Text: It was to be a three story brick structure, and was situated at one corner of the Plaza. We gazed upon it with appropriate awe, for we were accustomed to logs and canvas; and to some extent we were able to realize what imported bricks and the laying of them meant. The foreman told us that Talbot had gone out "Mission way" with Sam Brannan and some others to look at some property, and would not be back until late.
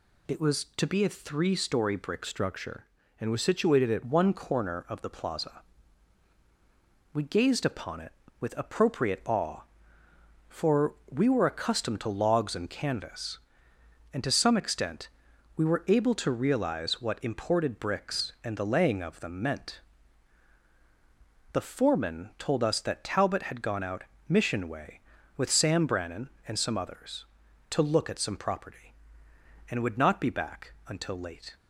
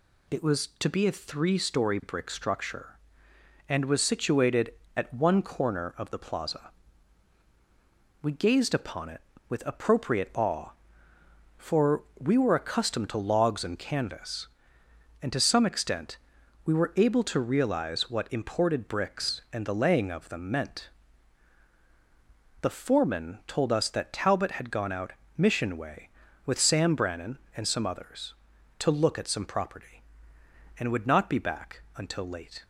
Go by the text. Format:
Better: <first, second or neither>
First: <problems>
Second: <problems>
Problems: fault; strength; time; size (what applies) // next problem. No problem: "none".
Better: second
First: changes voice from "structure" to "at"; from 2.2 to 4.0 s; 1.8 s long // pauses between "for" and "we"; slight; at 10.9 s; 0.16 s long // pauses between "extent" and "we"; noticeable; at 15.0 s; 0.48 s long // pauses between "out" and "Mission"; slight; at 24.0 s; 0.24 s long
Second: pauses between "for" and "we"; slight; at 12.0 s; 0.16 s long // pauses between "extent" and "we"; noticeable; at 16.1 s; 0.48 s long // pauses between "out" and "Mission"; slight; at 25.1 s; 0.24 s long